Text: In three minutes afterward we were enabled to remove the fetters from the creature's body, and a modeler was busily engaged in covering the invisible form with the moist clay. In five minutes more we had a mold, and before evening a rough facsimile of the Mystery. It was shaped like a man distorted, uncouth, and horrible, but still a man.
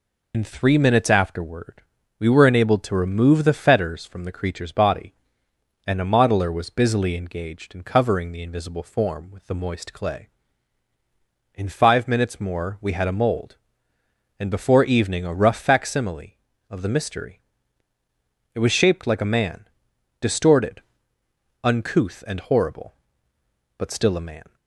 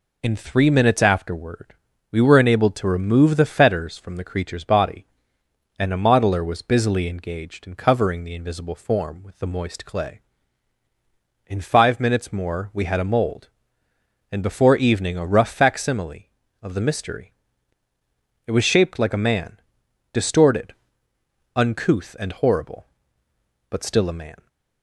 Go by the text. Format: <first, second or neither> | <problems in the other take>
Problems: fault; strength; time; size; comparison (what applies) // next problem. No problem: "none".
second | loses the start of "In"; at 0.3 s; 35 ms // pauses between "afterward" and "we"; slight; at 1.8 s; 0.36 s long; slight in the second // pauses between "man" and "distorted"; noticeable; at 19.6 s; 0.52 s long; noticeable in the second